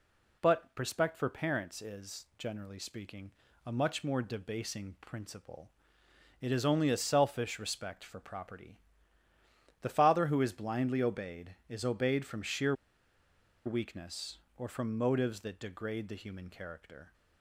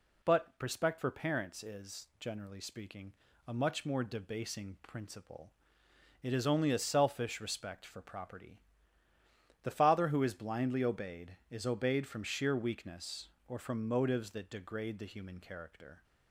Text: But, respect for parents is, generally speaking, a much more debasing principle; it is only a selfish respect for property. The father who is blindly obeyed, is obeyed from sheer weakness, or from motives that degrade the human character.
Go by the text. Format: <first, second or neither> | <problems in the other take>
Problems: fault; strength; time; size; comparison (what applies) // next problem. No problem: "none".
second | pauses between "sheer" and "weakness"; noticeable; at 12.7 s; 0.92 s long